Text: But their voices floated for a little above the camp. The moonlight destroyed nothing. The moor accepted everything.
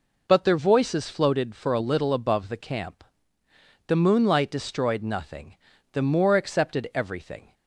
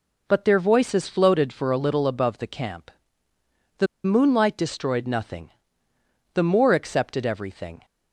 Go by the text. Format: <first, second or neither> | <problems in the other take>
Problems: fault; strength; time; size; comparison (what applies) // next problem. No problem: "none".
first | pauses between "The" and "moonlight"; slight; at 3.8 s; 0.18 s long